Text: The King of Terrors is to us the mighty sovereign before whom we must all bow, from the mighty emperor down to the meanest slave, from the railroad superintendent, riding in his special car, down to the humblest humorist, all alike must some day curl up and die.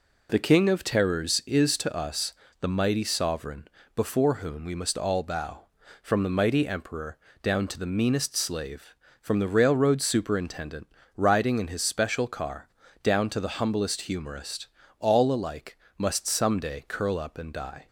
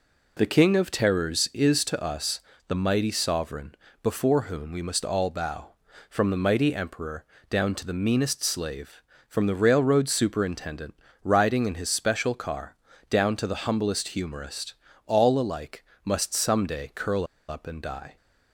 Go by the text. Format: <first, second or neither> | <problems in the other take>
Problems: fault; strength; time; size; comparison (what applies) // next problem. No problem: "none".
first | pauses between "us" and "the"; slight; at 2.4 s; 0.26 s long; slight in the first // pauses between "sovereign" and "before"; slight; at 3.7 s; 0.30 s long; slight in the first // pauses between "emperor" and "down"; slight; at 7.2 s; 0.26 s long; slight in the first // pauses between "alike" and "must"; slight; at 15.8 s; 0.20 s long; slight in the first // pauses between "curl" and "up"; slight; at 17.2 s; 0.22 s long